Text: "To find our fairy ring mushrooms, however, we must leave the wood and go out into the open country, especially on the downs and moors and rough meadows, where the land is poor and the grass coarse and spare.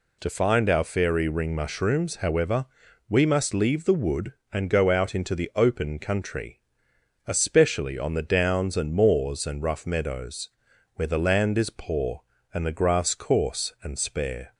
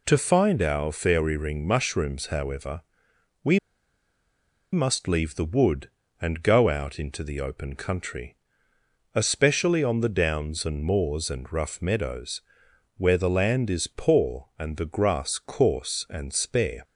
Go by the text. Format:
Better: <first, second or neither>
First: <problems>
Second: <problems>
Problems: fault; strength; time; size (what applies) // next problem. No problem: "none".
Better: first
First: none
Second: pauses between "we" and "must"; at 3.5 s; 1.1 s long